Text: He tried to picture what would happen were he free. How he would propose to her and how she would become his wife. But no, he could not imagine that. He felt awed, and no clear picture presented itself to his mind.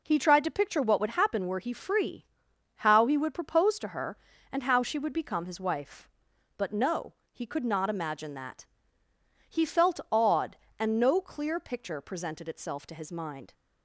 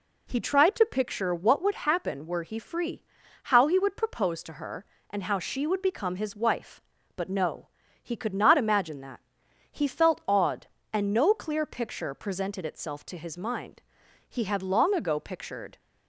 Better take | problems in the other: first | goes on to say "He had long ago pictured"; from 14.2 s on; 1.5 s long

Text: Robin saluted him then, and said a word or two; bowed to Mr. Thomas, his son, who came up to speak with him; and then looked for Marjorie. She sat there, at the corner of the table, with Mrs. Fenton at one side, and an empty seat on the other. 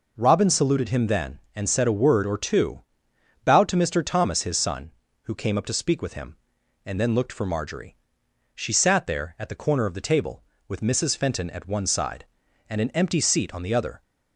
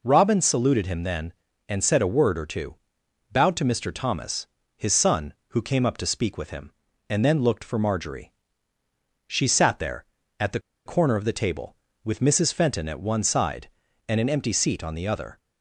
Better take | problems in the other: first | pauses between "the" and "corner"; slight; at 10.5 s; 0.26 s long

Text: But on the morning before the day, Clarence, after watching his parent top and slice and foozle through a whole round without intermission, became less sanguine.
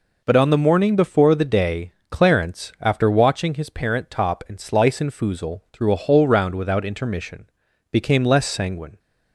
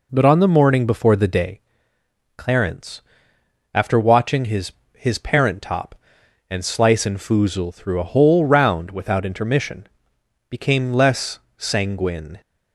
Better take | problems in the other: first | says "his" twice; at 4.9 s // pauses between "less" and "sanguine"; slight; at 11.3 s; 0.18 s long

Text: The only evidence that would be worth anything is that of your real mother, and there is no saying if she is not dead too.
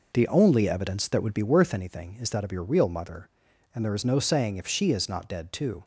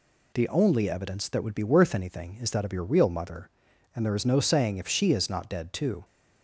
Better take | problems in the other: second | starts louder than the rest; noticeable; until 1.6 s; 5 dB

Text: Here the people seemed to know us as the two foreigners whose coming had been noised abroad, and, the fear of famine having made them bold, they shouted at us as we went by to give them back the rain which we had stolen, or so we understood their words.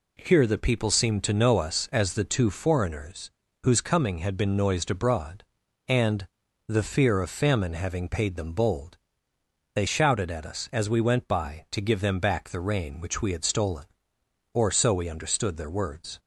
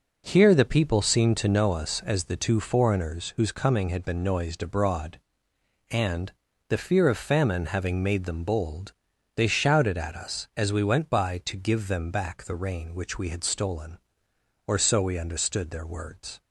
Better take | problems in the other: second | pauses between "foreigners" and "whose"; slight; at 3.2 s; 0.34 s long // says "paid" for "made"; at 8.0 s

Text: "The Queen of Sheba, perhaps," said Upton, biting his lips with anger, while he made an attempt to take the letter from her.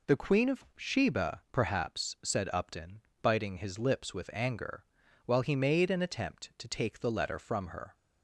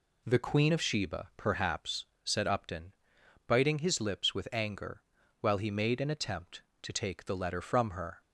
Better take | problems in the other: neither | none

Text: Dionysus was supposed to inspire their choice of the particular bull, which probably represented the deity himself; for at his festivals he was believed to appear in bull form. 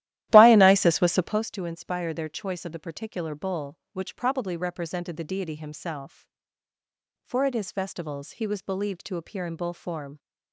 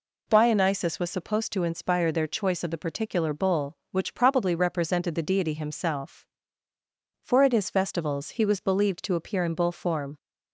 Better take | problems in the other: second | starts louder than the rest; strong; until 1.5 s; 14 dB

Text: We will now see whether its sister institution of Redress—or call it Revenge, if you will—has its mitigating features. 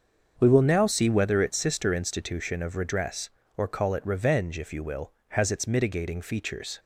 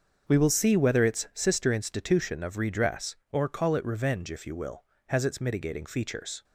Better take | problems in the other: first | starts louder than the rest; until 1.2 s; 7 dB; also in the first // skips "now"; at 0.4 s

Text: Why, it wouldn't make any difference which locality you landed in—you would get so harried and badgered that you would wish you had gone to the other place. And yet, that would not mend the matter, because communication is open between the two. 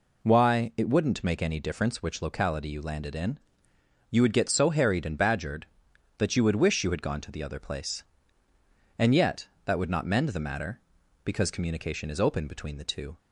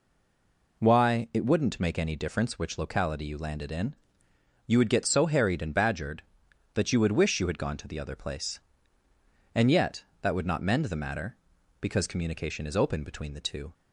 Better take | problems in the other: first | stays silent before the first word; slight; until 0.7 s; 0.7 s long

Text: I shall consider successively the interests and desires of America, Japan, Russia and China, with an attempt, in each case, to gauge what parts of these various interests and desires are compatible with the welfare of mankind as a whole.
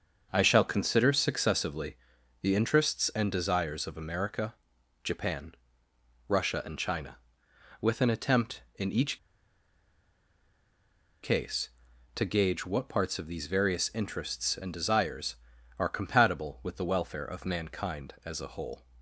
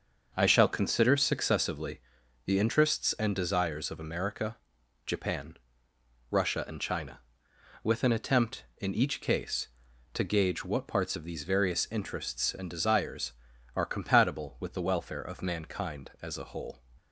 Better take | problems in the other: second | starts louder than the rest; until 1.3 s; 6.5 dB; also in the second // pauses between "successively" and "the"; noticeable; at 1.9 s; 0.46 s long; noticeable in the second // pauses between "each" and "case"; strong; at 9.1 s; 2.0 s long

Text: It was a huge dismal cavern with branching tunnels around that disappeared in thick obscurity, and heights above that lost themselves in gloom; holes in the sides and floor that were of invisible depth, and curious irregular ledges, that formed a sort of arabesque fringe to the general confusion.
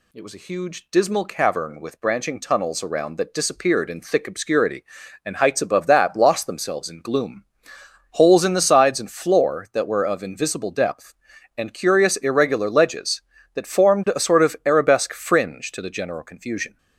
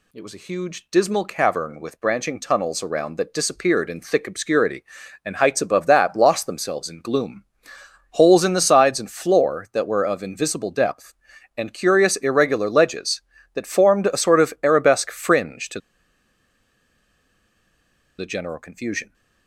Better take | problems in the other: first | pauses between "to" and "the"; strong; at 15.7 s; 2.3 s long

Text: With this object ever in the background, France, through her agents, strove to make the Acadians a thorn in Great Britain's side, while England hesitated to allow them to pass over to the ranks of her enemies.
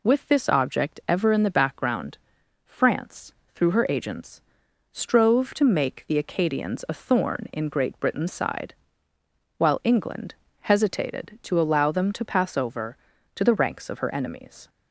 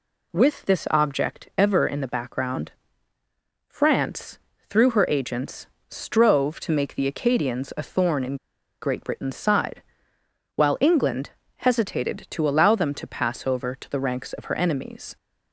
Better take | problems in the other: first | pauses between "in" and "Great"; noticeable; at 8.3 s; 0.45 s long // pauses between "England" and "hesitated"; slight; at 11.2 s; 0.28 s long; slight in the first

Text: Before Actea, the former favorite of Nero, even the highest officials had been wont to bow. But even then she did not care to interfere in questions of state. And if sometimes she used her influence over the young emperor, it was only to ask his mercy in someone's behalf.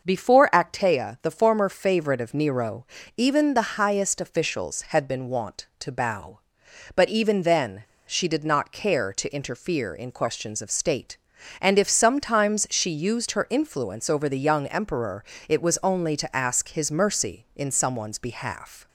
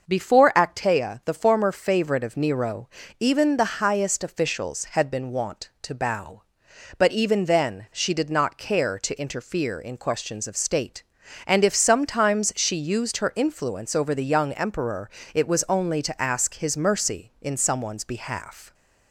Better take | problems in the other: second | starts louder than the rest; noticeable; until 1.0 s; 6 dB; noticeable in the second // pauses between "then" and "she"; slight; at 7.8 s; 0.23 s long

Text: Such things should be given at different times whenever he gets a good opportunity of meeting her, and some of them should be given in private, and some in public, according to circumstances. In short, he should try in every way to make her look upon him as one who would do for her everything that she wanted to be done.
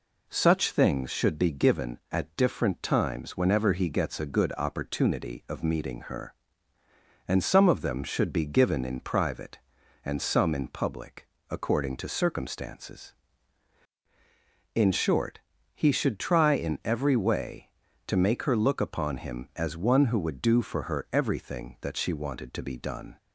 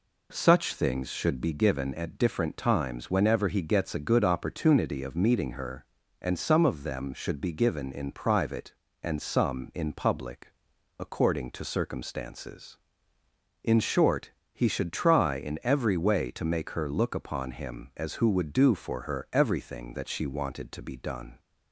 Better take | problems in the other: first | skips "one"; at 18.1 s

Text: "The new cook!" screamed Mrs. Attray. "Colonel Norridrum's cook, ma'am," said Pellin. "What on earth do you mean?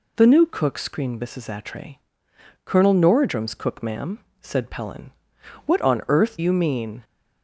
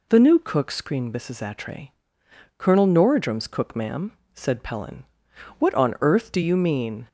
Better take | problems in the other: second | skips "do"; at 6.3 s

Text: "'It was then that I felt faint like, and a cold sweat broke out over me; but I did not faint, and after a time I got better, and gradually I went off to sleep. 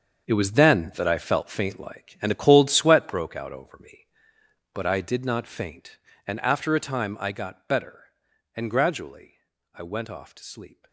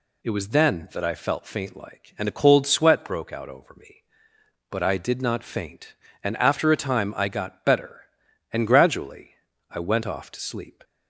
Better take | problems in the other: second | gets quieter; strong; throughout; 12.5 dB // pauses between "gradually" and "I"; slight; at 9.3 s; 0.34 s long; slight in the second

